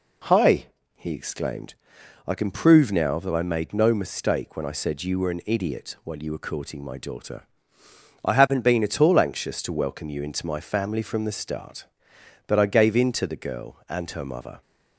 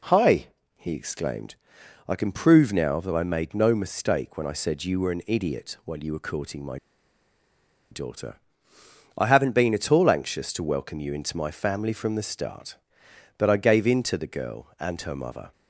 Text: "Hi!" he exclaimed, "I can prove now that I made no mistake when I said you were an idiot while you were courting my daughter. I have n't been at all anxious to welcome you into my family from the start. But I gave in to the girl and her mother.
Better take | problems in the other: first | pauses between "my" and "daughter"; at 6.7 s; 1.1 s long

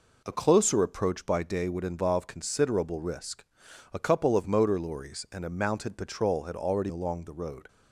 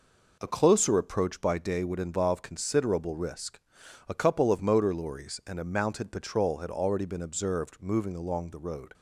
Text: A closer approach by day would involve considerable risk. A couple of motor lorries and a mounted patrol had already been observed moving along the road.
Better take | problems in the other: second | skips "been observed moving"; at 6.8 s

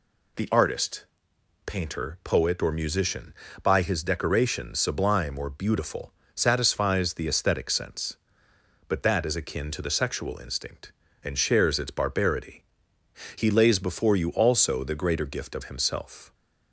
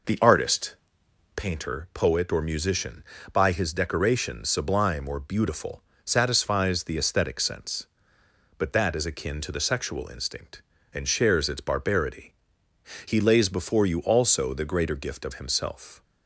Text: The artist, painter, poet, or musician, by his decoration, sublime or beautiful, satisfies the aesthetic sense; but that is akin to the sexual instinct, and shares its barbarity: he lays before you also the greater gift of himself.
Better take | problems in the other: first | starts louder than the rest; noticeable; until 1.5 s; 5 dB

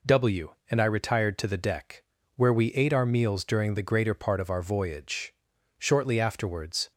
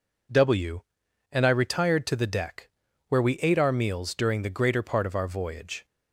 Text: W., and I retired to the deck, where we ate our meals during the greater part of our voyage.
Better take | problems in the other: second | goes on to say "Shortly afterwards"; noticeable; from 5.7 s on; 1.1 s long

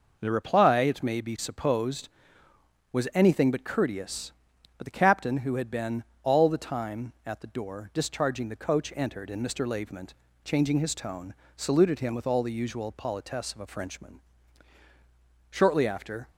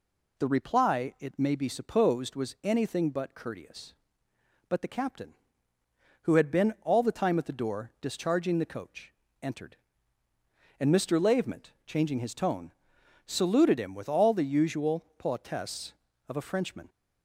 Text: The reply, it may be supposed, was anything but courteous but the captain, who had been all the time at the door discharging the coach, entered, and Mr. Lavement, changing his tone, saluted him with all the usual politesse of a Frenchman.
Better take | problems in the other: second | pauses between "been" and "all"; slight; at 6.0 s; 0.20 s long // goes on to say "Shortly after"; noticeable; from 15.4 s on; 0.80 s long

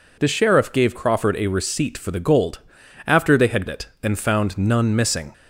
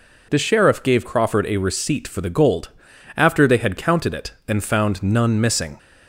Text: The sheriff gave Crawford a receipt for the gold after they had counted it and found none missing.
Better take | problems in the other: second | pauses between "gold" and "after"; noticeable; at 2.5 s; 0.46 s long; noticeable in the second // skips "counted"; at 3.6 s

